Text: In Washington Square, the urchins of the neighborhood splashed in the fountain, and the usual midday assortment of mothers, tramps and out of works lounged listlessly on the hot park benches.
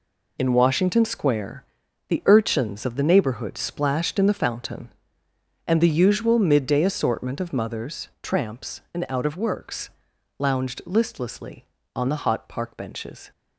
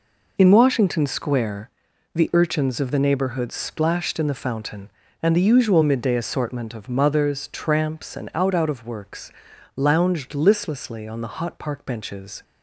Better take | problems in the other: first | says "out" twice; at 8.5 s // pauses between "works" and "lounged"; noticeable; at 9.3 s; 0.46 s long; noticeable in the first

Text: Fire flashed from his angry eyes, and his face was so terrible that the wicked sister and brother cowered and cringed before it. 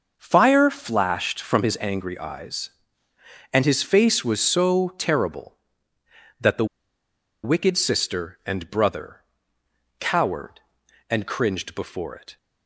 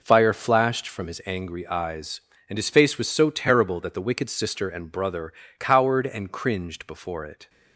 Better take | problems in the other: second | pauses between "the" and "wicked"; noticeable; at 6.6 s; 0.78 s long // pauses between "brother" and "cowered"; noticeable; at 9.2 s; 0.78 s long; slight in the second

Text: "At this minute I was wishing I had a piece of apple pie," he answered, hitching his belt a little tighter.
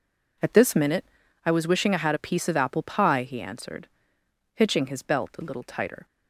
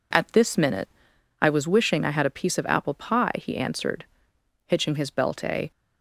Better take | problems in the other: first | pauses between "minute" and "I"; noticeable; at 0.8 s; 0.50 s long; also in the first // stops before "little tighter"; at 5.7 s

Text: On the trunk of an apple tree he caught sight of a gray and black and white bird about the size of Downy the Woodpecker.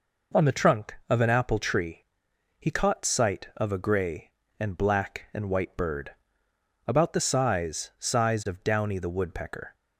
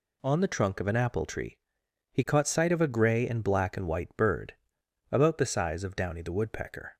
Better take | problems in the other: second | pauses between "tree" and "he"; noticeable; at 2.0 s; 0.52 s long; noticeable in the second // pauses between "bird" and "about"; noticeable; at 6.1 s; 0.74 s long; noticeable in the second // says "size" twice; at 7.9 s

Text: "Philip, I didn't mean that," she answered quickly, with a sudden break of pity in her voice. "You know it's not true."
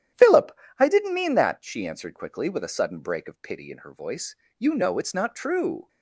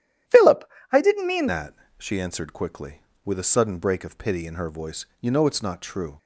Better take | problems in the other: first | starts louder than the rest; strong; until 1.5 s; 11.5 dB; strong in the first // changes voice at "that"; from 1.4 s on; 4.7 s long

